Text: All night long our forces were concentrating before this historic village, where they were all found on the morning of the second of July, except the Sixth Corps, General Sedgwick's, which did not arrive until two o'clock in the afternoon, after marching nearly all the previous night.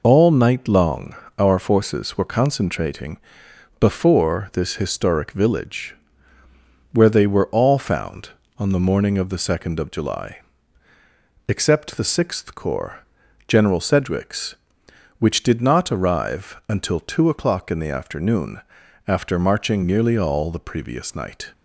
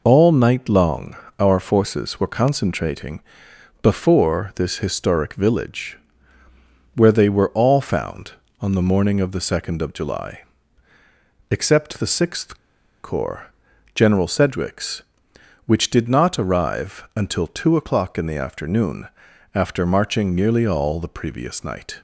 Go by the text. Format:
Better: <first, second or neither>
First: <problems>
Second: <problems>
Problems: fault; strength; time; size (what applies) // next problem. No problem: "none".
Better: first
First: pauses between "long" and "our"; slight; at 1.1 s; 0.24 s long // pauses between "concentrating" and "before"; noticeable; at 3.1 s; 0.60 s long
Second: pauses between "long" and "our"; slight; at 1.1 s; 0.24 s long // pauses between "concentrating" and "before"; noticeable; at 3.2 s; 0.60 s long // pauses between "Sixth" and "Corps"; noticeable; at 12.5 s; 0.46 s long